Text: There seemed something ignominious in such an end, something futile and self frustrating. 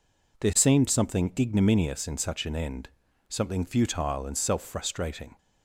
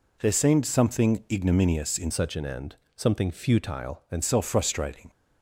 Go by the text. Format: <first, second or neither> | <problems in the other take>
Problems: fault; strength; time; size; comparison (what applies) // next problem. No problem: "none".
first | changes voice from "such" to "and"; from 2.1 to 4.2 s; 2.1 s long